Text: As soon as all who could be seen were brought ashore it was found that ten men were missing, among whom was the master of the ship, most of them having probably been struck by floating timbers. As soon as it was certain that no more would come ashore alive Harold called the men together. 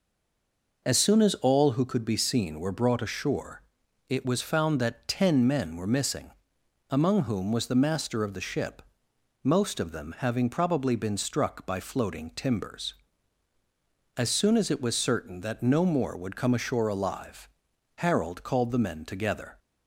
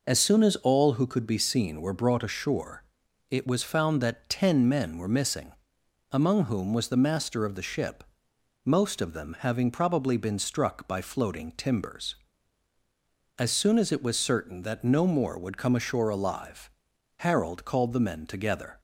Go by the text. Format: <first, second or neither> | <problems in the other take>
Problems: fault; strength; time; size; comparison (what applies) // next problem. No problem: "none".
second | stays silent before the first word; slight; until 0.8 s; 0.8 s long // pauses between "ashore" and "it"; noticeable; at 3.6 s; 0.46 s long; noticeable in the second // pauses between "alive" and "Harold"; noticeable; at 17.4 s; 0.52 s long; noticeable in the second